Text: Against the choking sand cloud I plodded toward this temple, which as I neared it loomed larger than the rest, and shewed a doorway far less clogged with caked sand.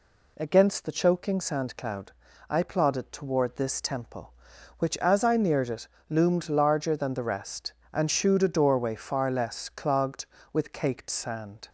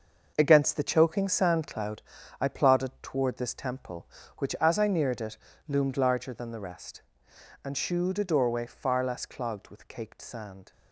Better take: first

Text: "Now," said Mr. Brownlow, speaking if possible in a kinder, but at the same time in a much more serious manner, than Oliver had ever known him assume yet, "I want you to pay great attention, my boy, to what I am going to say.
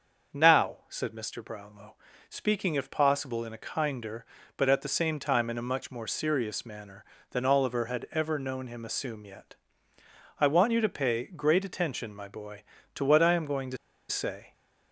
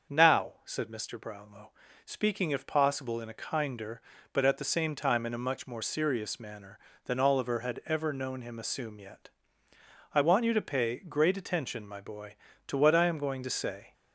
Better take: second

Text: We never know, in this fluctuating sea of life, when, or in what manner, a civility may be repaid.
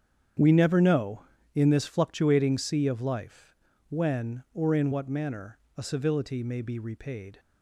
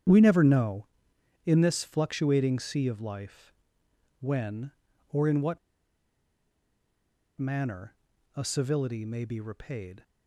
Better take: first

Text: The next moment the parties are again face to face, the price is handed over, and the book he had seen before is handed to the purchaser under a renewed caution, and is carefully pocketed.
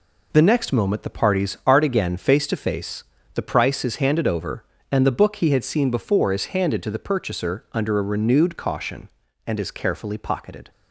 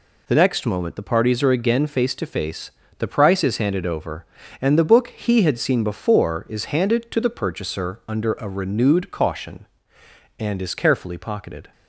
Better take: second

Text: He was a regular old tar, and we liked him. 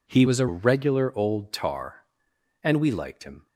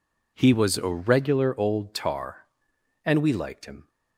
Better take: second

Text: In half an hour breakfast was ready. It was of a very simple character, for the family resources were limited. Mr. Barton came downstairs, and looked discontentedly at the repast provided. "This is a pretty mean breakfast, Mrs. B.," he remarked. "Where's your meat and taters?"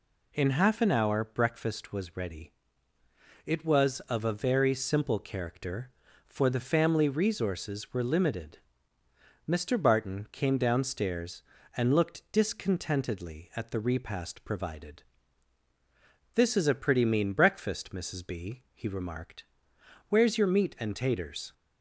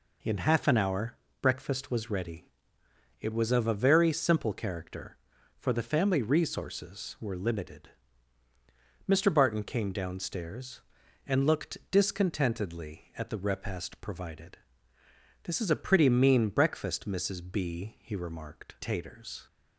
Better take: first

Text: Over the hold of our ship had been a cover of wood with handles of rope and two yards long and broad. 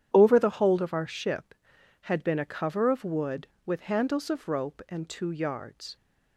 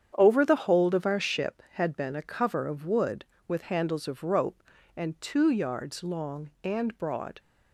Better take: second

